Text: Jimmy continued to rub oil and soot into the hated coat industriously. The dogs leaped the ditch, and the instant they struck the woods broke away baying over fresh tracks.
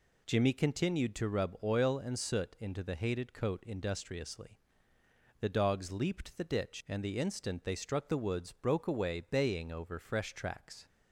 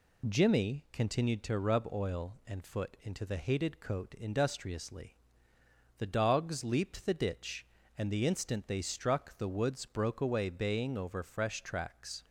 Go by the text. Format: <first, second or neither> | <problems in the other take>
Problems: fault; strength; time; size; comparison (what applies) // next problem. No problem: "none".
first | says "foot" for "soot"; at 2.6 s